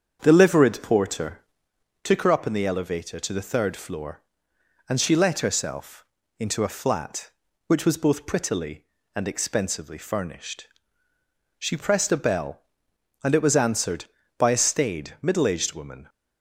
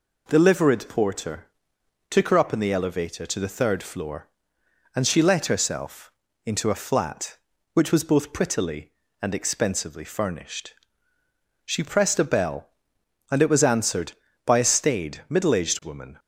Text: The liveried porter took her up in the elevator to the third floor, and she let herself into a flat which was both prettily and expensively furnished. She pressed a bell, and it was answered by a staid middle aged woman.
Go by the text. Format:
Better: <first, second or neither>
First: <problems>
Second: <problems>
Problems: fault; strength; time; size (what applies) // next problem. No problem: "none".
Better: second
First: starts louder than the rest; strong; until 1.7 s; 7.5 dB // pauses between "porter" and "took"; noticeable; at 1.3 s; 0.64 s long // pauses between "herself" and "into"; slight; at 6.0 s; 0.34 s long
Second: pauses between "porter" and "took"; noticeable; at 1.4 s; 0.64 s long // pauses between "herself" and "into"; slight; at 6.0 s; 0.34 s long